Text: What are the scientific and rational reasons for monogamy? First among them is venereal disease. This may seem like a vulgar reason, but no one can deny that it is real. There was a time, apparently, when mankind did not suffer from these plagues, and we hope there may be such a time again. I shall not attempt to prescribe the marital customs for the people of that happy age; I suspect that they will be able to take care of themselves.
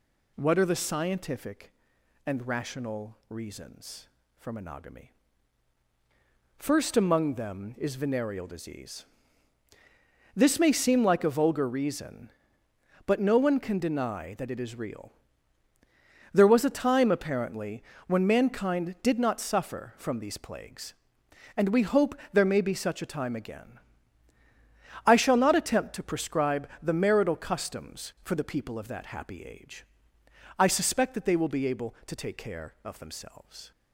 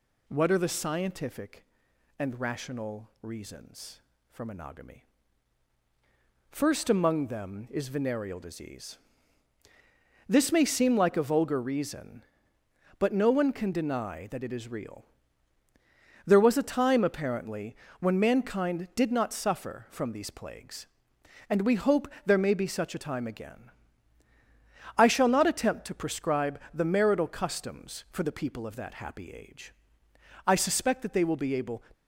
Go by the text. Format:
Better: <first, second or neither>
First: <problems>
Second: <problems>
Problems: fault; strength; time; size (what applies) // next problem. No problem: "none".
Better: first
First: pauses between "hope" and "there"; slight; at 22.1 s; 0.16 s long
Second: pauses between "hope" and "there"; slight; at 22.0 s; 0.16 s long // stops before "to take care of themselves"; at 31.9 s